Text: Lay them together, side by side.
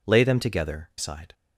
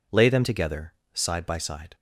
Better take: second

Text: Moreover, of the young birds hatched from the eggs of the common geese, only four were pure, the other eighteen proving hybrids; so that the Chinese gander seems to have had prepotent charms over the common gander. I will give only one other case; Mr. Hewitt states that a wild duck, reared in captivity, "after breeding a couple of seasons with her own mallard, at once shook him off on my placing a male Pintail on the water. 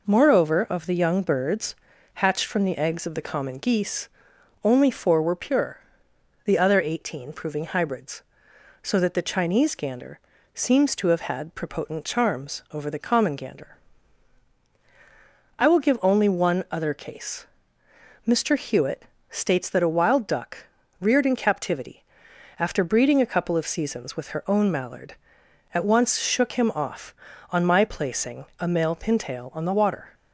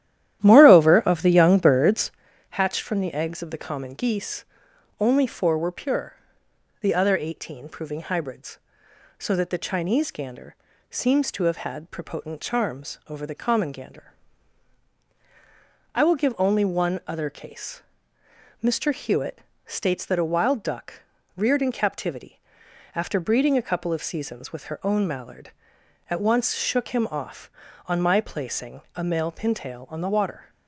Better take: first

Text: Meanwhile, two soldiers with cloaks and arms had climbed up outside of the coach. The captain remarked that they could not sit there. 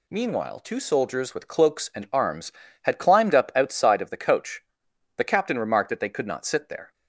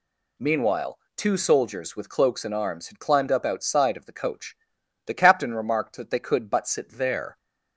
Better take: first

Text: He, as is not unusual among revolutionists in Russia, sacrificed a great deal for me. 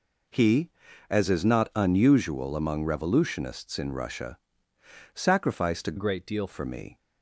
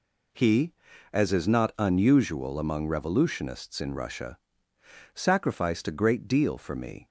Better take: second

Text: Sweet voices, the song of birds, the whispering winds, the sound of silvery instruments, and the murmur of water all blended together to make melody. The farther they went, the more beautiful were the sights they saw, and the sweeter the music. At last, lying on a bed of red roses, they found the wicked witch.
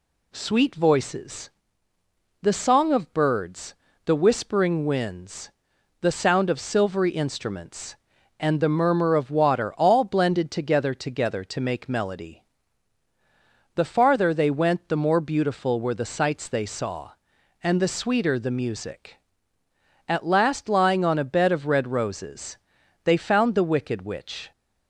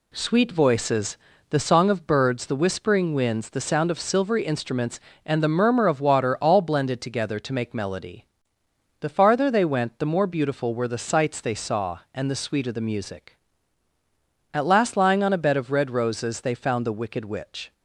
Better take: second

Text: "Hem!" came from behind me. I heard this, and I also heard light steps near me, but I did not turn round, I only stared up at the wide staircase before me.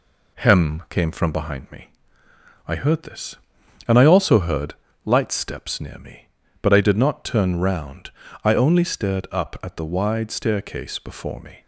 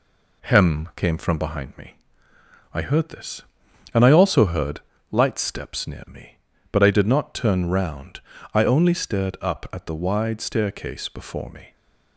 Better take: neither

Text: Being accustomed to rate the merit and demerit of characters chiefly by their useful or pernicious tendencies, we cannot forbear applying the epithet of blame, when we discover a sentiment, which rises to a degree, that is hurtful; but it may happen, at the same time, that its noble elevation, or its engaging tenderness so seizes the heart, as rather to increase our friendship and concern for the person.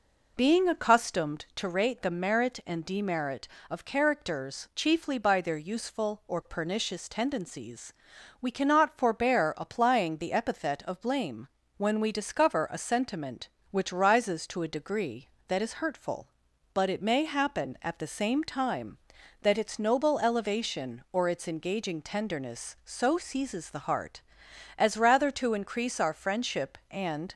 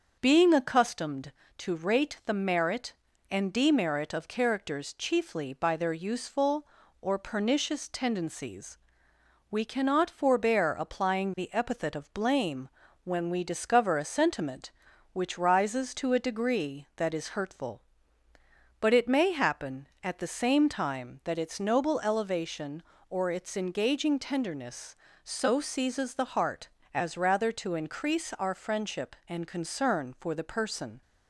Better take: second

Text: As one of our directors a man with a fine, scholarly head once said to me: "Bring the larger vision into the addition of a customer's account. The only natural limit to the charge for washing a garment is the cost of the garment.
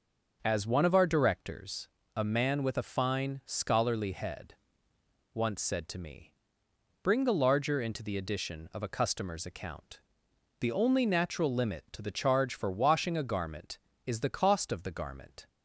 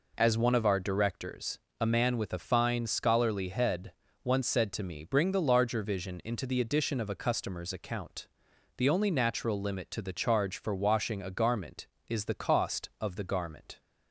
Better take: second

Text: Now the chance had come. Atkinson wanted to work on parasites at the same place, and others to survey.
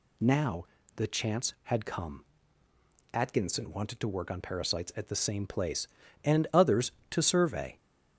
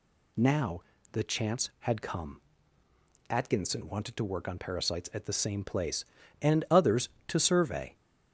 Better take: neither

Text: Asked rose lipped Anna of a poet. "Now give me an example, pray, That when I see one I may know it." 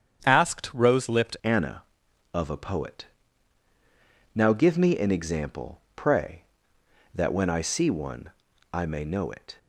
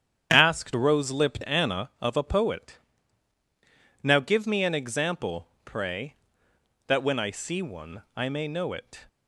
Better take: second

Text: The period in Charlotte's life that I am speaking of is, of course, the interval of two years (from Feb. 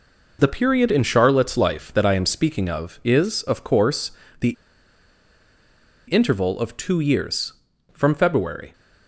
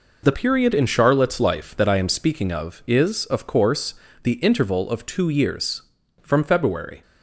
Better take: second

